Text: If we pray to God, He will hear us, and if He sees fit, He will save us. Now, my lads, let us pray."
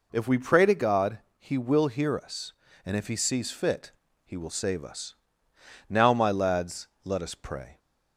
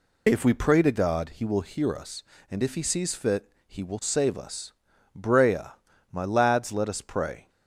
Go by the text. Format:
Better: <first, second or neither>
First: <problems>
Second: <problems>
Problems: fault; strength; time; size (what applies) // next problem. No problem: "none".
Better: first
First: none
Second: says "Brea" for "Now"; at 5.1 s